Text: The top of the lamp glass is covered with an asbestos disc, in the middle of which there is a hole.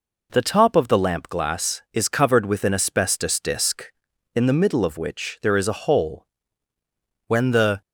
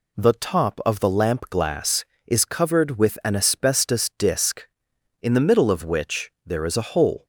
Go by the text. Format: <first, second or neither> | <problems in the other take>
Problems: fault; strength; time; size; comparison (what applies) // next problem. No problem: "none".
second | goes on to say "When the"; from 7.2 s on; 0.54 s long